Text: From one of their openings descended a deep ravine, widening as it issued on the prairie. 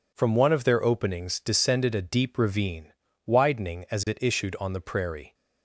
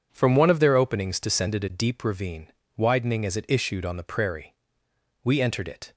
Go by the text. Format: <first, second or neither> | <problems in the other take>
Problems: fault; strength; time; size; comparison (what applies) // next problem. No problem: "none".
first | goes on to say "We entered it"; noticeable; from 5.2 s on; 0.70 s long